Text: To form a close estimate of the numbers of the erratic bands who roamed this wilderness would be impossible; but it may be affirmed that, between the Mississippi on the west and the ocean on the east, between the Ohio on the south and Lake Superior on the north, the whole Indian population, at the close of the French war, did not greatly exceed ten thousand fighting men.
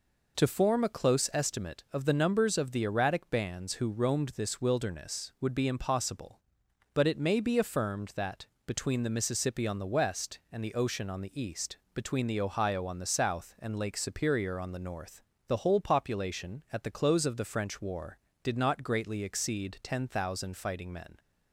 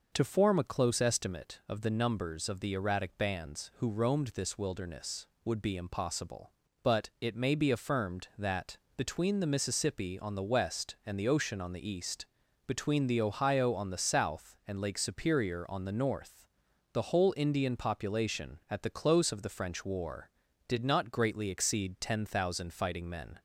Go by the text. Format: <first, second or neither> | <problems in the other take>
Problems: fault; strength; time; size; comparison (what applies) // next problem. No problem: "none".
second | skips "Indian"; at 15.7 s